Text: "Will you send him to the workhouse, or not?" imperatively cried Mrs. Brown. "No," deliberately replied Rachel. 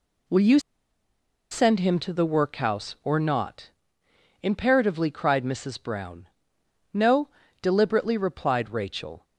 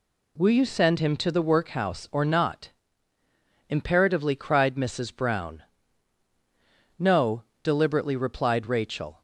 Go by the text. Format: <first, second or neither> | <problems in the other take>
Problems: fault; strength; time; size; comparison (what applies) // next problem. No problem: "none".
second | pauses between "you" and "send"; noticeable; at 0.5 s; 0.92 s long